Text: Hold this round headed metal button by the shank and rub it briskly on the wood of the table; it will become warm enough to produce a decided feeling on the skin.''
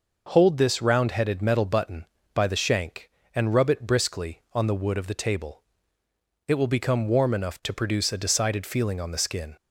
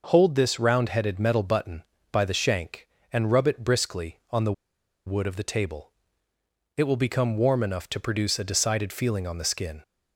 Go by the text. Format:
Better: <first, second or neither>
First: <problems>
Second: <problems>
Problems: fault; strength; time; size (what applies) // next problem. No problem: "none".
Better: first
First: none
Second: pauses between "the" and "wood"; noticeable; at 4.5 s; 0.53 s long